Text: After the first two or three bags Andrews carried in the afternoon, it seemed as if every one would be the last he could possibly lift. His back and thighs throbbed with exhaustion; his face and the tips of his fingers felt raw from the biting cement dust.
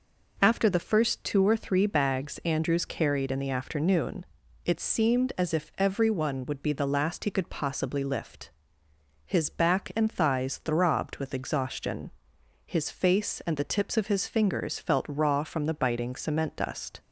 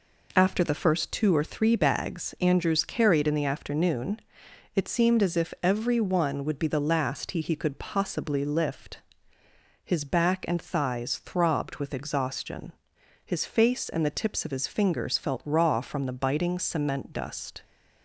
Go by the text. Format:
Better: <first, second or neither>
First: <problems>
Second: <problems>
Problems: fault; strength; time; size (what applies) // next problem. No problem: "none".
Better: first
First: none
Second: says "he" twice; at 7.4 s